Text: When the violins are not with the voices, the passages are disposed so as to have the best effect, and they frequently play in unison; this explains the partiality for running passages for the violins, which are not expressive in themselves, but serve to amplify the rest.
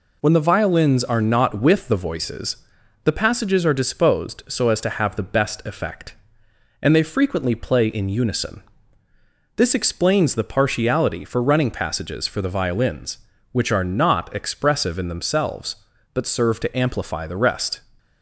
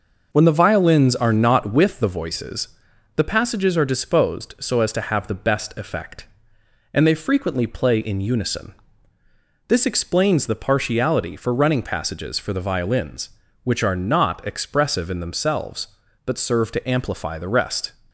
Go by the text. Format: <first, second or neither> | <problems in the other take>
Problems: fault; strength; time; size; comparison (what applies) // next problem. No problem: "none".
first | starts louder than the rest; noticeable; until 1.8 s; 5.5 dB